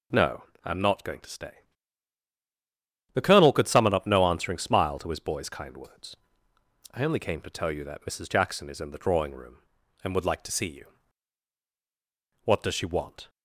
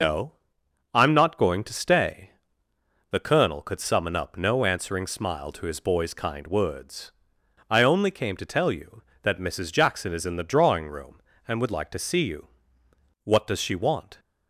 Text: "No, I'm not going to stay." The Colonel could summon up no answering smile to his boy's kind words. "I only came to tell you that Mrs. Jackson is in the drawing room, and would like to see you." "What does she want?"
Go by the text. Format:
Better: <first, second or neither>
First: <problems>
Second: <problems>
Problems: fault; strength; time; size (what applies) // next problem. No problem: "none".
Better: first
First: none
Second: loses the start of "No"; at 0.0 s; 75 ms